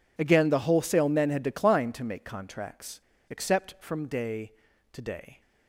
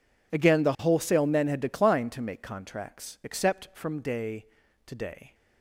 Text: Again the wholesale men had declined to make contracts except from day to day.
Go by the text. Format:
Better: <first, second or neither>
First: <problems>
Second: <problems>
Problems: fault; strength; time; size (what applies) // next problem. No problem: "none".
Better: second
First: pauses between "contracts" and "except"; slight; at 3.0 s; 0.27 s long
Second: none